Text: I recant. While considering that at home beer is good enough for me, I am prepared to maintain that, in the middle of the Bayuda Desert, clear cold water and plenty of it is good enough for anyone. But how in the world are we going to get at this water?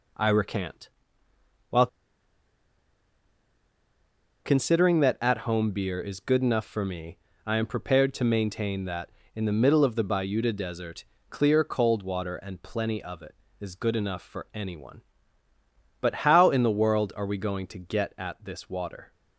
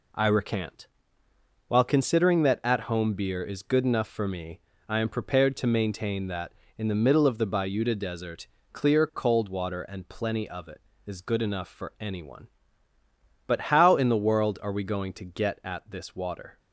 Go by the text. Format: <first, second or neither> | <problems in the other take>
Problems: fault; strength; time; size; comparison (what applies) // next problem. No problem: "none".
second | pauses between "While" and "considering"; strong; at 1.8 s; 2.5 s long